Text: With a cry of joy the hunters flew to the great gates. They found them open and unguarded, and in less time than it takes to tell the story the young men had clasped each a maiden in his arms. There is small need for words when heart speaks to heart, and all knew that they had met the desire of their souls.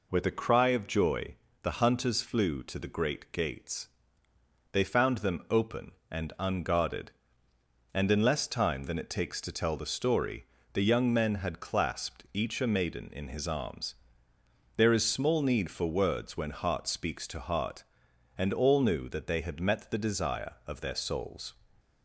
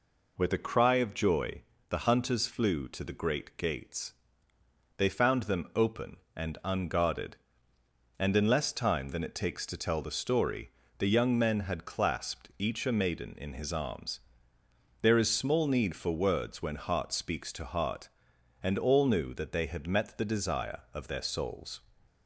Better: neither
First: pauses between "joy" and "the"; slight; at 1.3 s; 0.26 s long // pauses between "story" and "the"; slight; at 10.4 s; 0.28 s long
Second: pauses between "joy" and "the"; slight; at 1.6 s; 0.26 s long // pauses between "story" and "the"; slight; at 10.6 s; 0.28 s long

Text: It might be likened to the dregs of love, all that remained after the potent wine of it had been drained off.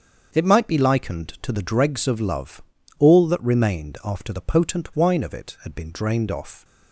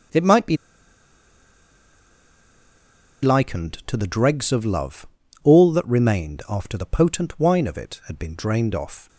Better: first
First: starts louder than the rest; until 1.4 s; 7 dB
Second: starts louder than the rest; until 3.9 s; 7 dB // pauses between "be" and "likened"; strong; at 0.5 s; 2.6 s long

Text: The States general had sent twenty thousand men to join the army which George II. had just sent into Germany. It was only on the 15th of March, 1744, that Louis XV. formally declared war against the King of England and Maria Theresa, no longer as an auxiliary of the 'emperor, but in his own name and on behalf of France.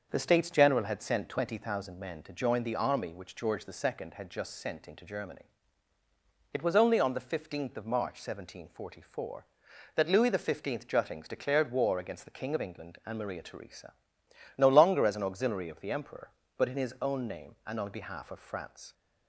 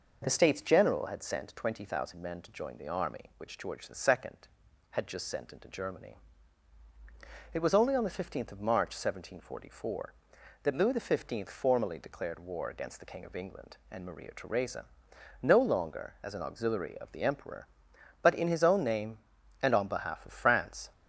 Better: second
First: starts louder than the rest; until 1.1 s; 6.5 dB // says "juttings" for "formally"; at 10.8 s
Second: none

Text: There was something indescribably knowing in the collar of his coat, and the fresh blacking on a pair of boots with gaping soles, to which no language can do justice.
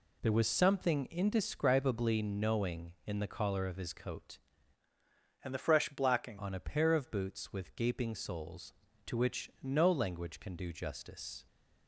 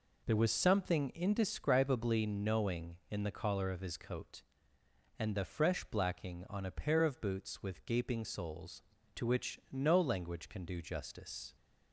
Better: second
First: changes voice from "and" to "blacking"; from 5.4 to 6.3 s; 0.9 s long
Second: none

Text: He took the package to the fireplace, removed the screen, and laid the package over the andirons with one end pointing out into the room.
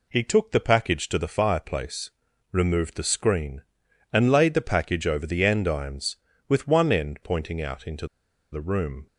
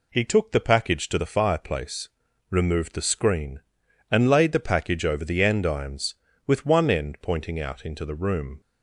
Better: second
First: pauses between "into" and "the"; noticeable; at 8.0 s; 0.46 s long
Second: none

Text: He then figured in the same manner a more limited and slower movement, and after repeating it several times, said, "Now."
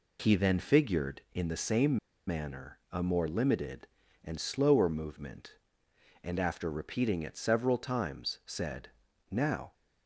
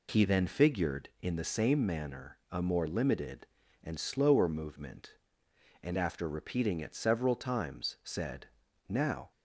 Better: second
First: pauses between "same" and "manner"; slight; at 1.9 s; 0.30 s long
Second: none

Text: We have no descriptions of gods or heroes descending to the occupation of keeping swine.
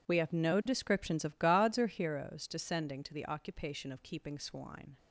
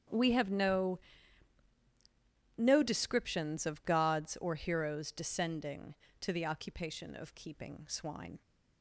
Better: first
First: none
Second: starts louder than the rest; strong; until 2.6 s; 8.5 dB // says "no" twice; at 2.5 s

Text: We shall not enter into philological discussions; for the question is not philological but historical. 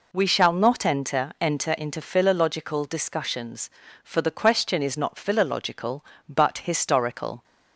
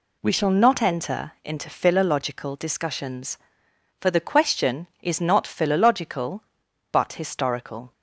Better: second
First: says "enter" twice; at 1.4 s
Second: none

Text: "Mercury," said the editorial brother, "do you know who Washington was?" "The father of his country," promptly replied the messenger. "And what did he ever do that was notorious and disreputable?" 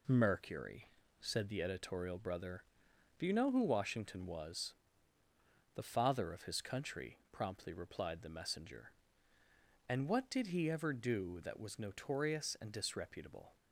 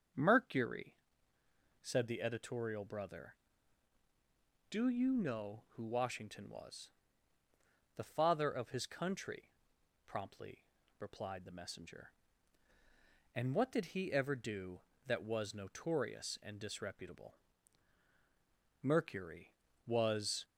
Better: first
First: none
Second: starts louder than the rest; strong; until 2.0 s; 7.5 dB // pauses between "promptly" and "replied"; slight; at 10.6 s; 0.32 s long // goes on to say "Mercury was"; from 18.8 s on; 1.6 s long

